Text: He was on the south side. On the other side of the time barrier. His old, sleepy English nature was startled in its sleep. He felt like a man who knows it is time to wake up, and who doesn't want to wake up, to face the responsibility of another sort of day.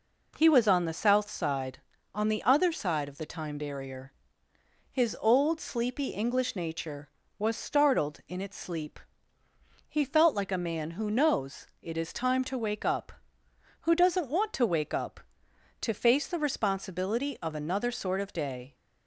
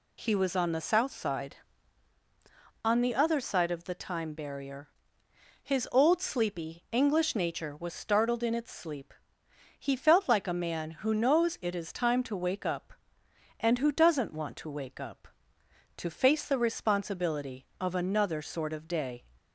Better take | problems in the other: second | pauses between "knows" and "it"; slight; at 11.6 s; 0.16 s long // skips "and"; at 13.4 s

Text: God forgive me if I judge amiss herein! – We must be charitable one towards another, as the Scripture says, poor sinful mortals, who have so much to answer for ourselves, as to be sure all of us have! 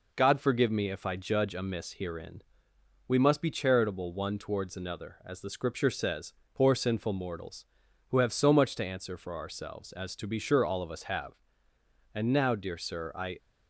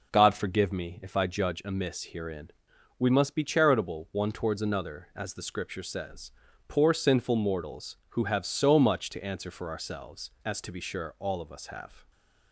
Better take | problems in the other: second | goes on to say "And now dear Sir I"; noticeable; from 12.1 s on; 1.2 s long

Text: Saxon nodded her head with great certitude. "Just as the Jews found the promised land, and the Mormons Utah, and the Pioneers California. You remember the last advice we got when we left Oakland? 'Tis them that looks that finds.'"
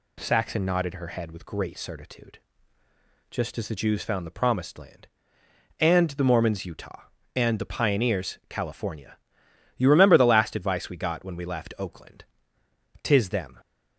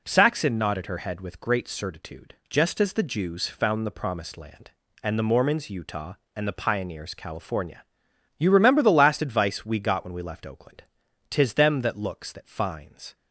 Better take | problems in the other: second | stops before "that looks that finds"; at 13.5 s

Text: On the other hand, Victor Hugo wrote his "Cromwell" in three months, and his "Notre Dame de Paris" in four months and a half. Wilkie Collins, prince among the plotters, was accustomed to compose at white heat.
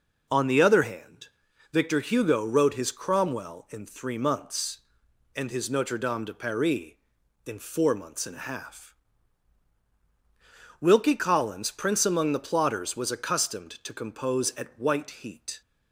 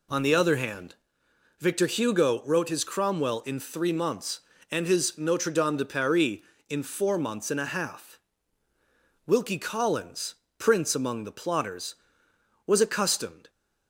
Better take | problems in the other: first | stops before "to compose at white heat"; at 13.4 s

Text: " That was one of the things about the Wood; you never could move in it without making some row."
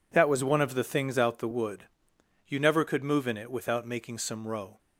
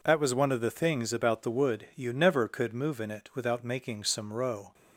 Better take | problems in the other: second | says "out" for "about"; at 1.1 s

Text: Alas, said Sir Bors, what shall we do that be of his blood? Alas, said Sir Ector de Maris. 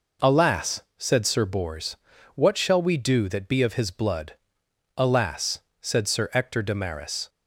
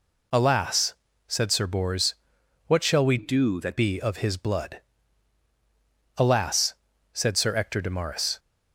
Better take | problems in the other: first | changes voice from "do" to "that"; from 3.1 to 3.7 s; 0.6 s long

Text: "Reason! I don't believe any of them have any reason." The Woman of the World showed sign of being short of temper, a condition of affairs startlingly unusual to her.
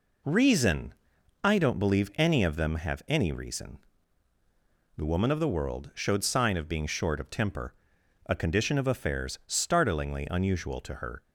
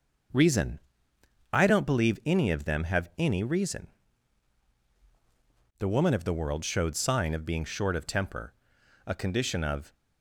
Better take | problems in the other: first | starts louder than the rest; until 2.0 s; 6.5 dB // stops before "affairs startlingly unusual to her"; at 9.9 s

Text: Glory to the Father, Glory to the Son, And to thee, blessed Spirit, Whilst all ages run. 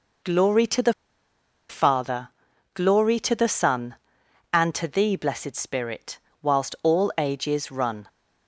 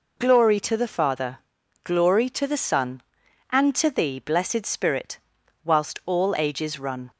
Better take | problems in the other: second | pauses between "the" and "Father"; noticeable; at 0.9 s; 0.77 s long

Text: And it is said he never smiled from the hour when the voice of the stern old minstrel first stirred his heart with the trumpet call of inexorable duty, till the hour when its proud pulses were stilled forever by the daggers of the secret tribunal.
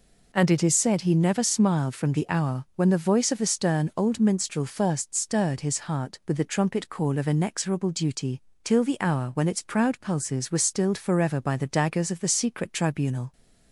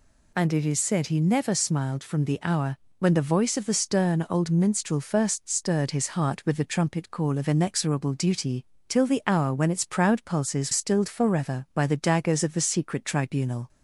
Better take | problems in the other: first | pauses between "hour" and "when"; slight; at 2.7 s; 0.20 s long // skips "were"; at 10.7 s

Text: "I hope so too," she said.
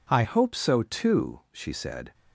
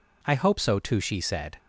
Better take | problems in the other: second | changes voice at "hope"; from 0.2 s on; 1.9 s long

